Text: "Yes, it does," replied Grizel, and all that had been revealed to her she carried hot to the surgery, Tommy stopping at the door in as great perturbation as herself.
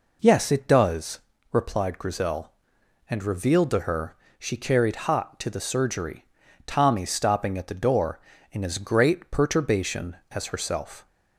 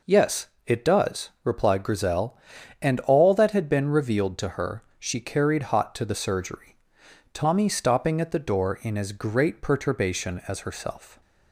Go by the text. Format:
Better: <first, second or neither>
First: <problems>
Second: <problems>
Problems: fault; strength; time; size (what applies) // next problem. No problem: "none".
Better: second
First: skips "all that had been"; at 3.2 s // pauses between "her" and "she"; slight; at 4.1 s; 0.22 s long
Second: pauses between "her" and "she"; slight; at 4.8 s; 0.16 s long